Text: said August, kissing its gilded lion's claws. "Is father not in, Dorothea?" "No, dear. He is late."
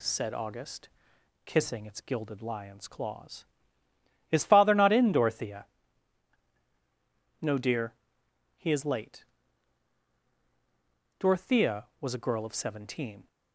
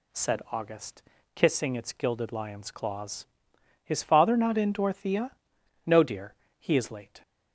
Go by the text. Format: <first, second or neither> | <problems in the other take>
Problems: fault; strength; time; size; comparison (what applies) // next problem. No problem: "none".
second | goes on to say "Dorothea was a girl of seventeen"; strong; from 11.1 s on; 2.0 s long